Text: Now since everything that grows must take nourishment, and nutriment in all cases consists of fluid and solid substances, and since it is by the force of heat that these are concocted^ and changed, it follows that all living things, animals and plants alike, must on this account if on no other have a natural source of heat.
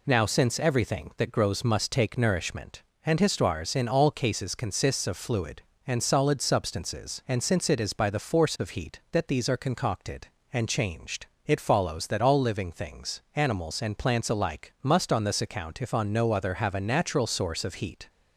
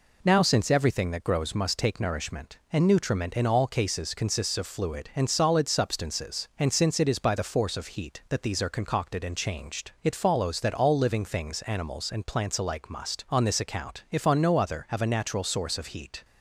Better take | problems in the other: second | says "histoires" for "nutriment"; at 3.2 s

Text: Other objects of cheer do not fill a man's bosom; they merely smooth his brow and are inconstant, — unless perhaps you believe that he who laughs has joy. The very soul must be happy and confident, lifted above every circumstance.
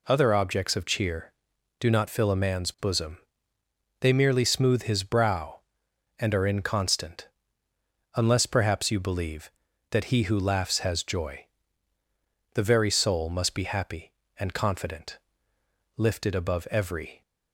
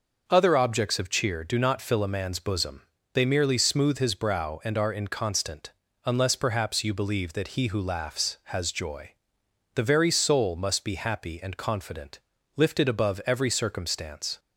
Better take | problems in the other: second | stops before "circumstance"; at 17.2 s

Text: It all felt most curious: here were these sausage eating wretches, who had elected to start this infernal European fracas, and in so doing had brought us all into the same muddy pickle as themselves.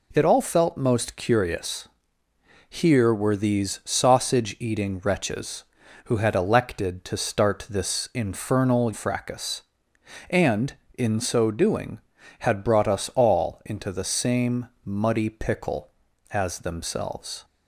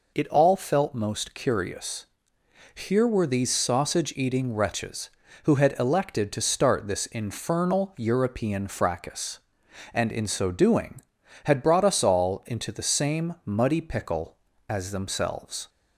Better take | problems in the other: second | skips "European"; at 8.9 s // pauses between "same" and "muddy"; slight; at 14.6 s; 0.16 s long

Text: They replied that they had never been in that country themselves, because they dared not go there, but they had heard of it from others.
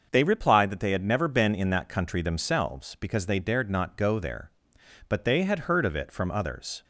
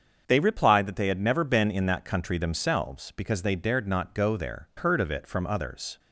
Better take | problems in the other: first | starts louder than the rest; until 1.2 s; 6.5 dB; noticeable in the first // skips "but they had"; at 4.7 s

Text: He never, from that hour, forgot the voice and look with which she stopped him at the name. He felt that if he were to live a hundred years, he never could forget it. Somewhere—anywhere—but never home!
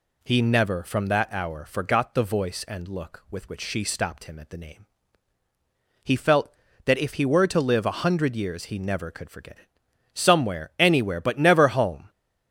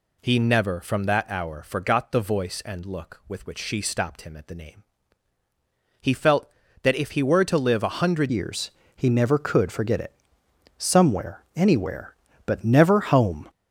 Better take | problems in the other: first | changes voice at "years"; from 8.2 s on; 5.2 s long

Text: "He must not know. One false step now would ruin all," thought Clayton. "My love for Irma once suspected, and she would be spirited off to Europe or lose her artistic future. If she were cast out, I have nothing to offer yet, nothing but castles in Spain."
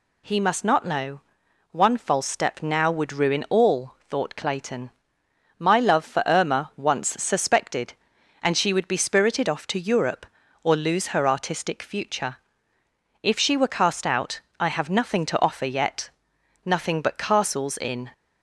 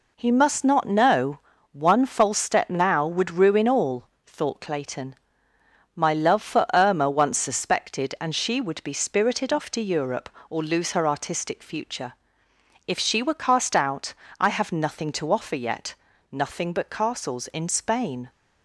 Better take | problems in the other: second | stops before "Spain"; at 18.1 s

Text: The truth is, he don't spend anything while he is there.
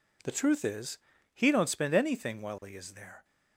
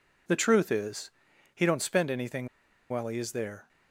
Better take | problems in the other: first | pauses between "anything" and "while"; at 2.4 s; 0.42 s long

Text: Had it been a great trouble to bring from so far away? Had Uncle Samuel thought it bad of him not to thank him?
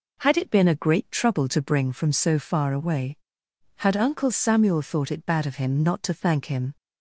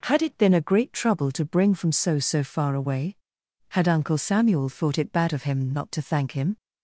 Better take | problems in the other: first | says "so" twice; at 2.1 s

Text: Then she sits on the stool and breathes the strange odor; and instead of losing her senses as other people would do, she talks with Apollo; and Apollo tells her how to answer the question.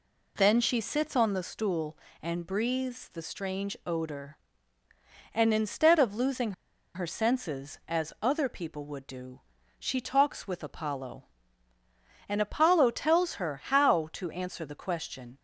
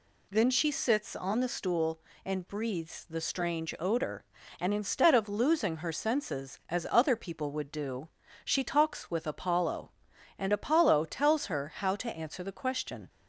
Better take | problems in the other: second | pauses between "losing" and "her"; at 6.5 s; 0.42 s long

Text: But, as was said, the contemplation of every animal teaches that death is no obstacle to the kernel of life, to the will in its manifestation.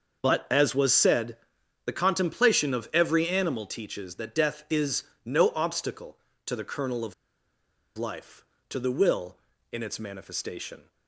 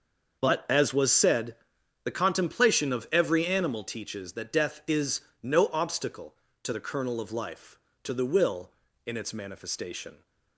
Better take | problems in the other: second | starts louder than the rest; until 1.2 s; 6.5 dB; also in the second // pauses between "is" and "no"; slight; at 5.0 s; 0.20 s long; slight in the second // pauses between "of" and "life"; noticeable; at 7.1 s; 0.83 s long

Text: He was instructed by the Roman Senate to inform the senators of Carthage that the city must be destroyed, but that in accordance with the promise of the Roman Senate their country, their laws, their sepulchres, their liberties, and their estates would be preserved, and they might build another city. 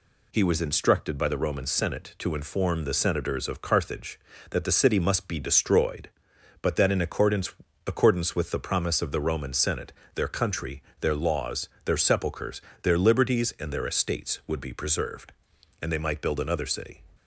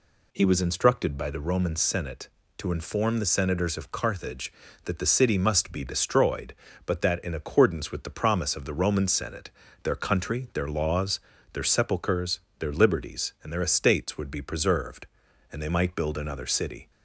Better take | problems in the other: second | says "accordance" twice; at 7.8 s // pauses between "Senate" and "their"; slight; at 9.9 s; 0.22 s long; slight in the second

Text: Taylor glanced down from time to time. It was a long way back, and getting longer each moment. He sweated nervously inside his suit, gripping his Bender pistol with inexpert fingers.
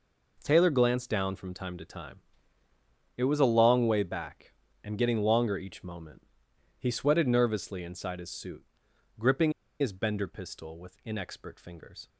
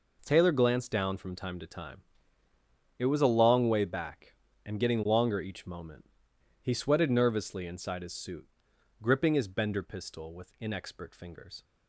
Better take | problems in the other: second | pauses between "gripping" and "his"; slight; at 9.5 s; 0.29 s long

